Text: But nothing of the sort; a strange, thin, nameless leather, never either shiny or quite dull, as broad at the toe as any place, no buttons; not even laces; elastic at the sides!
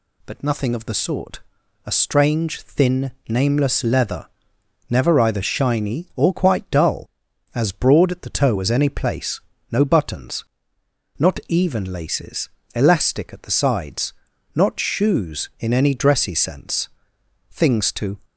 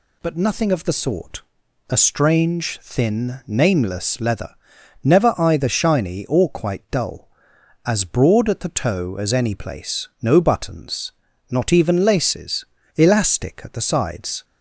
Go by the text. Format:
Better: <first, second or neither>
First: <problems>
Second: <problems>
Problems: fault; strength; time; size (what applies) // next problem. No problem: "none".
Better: second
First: goes on to say "Not shoes in any dressy sense Things to"; strong; from 14.5 s on; 3.6 s long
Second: none